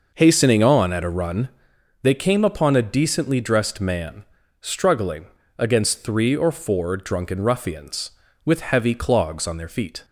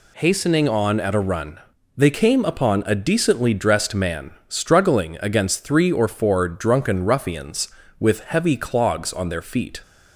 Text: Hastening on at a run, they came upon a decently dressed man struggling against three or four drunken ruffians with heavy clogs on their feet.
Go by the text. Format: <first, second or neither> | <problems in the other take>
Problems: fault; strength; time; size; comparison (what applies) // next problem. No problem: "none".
second | starts louder than the rest; noticeable; until 1.8 s; 5.5 dB // pauses between "man" and "struggling"; slight; at 4.2 s; 0.36 s long; slight in the second // pauses between "struggling" and "against"; slight; at 5.2 s; 0.32 s long